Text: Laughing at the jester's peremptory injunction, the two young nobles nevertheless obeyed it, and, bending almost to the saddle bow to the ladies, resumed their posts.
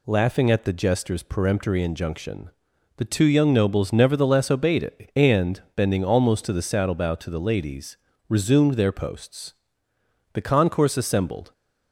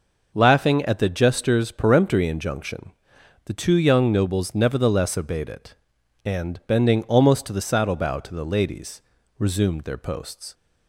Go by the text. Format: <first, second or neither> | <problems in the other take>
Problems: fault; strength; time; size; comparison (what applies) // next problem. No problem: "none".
second | goes on to say "The concourse assembled"; noticeable; from 10.3 s on; 1.1 s long